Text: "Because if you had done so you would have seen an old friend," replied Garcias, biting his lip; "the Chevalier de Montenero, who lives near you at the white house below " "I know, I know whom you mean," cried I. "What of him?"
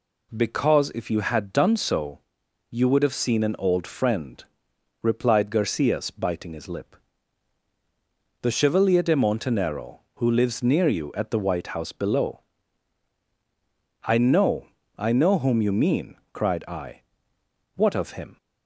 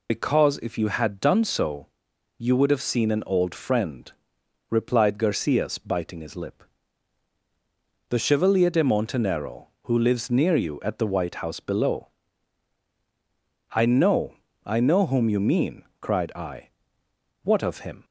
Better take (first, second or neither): first